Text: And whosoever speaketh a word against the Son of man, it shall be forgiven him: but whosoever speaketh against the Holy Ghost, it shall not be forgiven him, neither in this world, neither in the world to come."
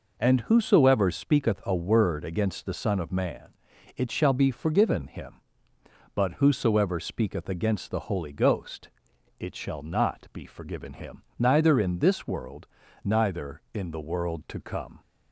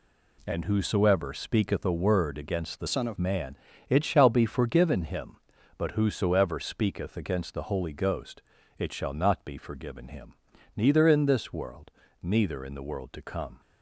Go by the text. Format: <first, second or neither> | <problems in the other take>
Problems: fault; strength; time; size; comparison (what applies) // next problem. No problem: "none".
first | changes voice from "Son" to "of"; from 2.8 to 3.1 s; 0.3 s long